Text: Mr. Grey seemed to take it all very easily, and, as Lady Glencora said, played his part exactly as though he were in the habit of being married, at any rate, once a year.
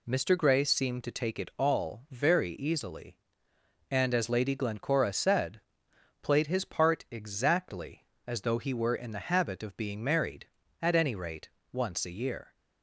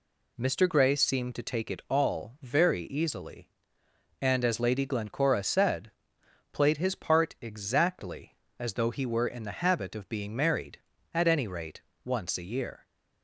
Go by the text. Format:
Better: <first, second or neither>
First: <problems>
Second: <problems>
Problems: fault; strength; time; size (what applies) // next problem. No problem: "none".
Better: neither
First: none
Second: none